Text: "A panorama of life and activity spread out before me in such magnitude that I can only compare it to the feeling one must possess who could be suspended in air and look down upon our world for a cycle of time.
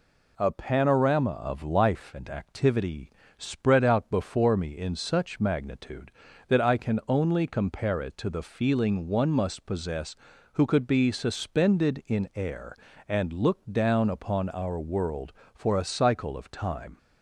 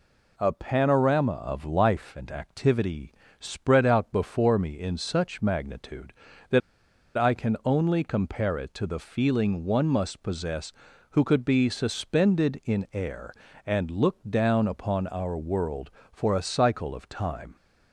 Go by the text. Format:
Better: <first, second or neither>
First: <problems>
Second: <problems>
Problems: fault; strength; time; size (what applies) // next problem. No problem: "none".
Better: first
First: pauses between "activity" and "spread"; slight; at 3.0 s; 0.30 s long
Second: pauses between "activity" and "spread"; slight; at 3.1 s; 0.30 s long // pauses between "that" and "I"; noticeable; at 6.6 s; 0.56 s long